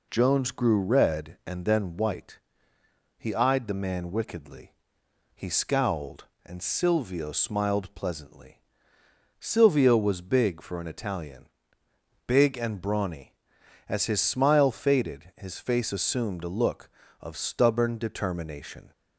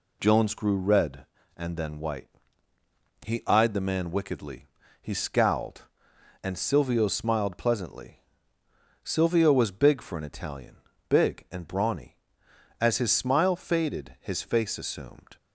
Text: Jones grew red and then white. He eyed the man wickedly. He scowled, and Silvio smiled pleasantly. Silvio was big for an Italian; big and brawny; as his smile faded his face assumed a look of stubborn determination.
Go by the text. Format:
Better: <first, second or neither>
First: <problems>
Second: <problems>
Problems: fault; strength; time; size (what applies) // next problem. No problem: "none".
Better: first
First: none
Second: stops before "a look of stubborn determination"; at 15.3 s